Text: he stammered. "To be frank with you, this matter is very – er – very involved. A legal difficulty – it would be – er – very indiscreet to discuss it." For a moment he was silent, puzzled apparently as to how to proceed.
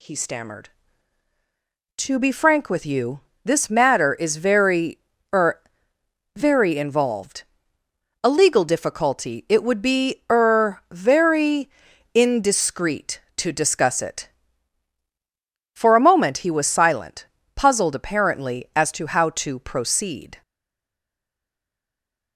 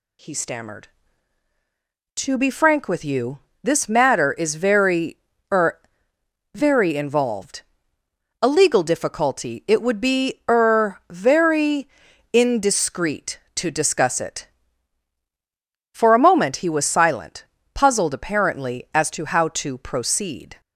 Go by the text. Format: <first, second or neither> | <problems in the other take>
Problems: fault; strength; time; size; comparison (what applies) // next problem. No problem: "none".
second | pauses between "very" and "indiscreet"; noticeable; at 11.6 s; 0.46 s long; noticeable in the second // stays silent after the last word; noticeable; from 20.4 s on; 1.9 s long